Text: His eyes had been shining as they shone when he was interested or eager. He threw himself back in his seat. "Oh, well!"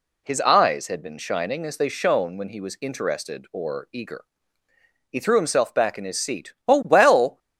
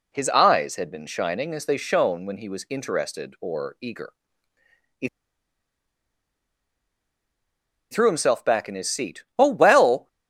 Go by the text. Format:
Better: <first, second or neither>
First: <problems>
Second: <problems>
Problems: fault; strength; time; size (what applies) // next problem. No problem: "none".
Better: first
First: none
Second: pauses between "He" and "threw"; strong; at 5.0 s; 2.8 s long